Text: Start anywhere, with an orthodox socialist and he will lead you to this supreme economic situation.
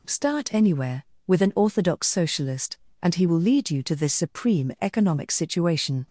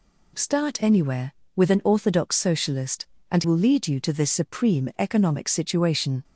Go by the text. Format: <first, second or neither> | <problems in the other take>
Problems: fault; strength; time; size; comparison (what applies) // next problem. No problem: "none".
first | skips "he"; at 3.4 s